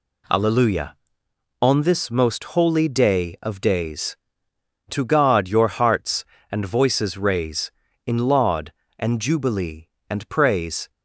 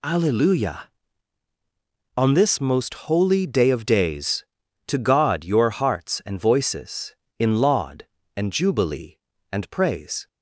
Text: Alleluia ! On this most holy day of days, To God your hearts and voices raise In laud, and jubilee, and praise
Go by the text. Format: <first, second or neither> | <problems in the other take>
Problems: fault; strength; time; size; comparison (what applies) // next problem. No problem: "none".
first | skips "raise"; at 7.2 s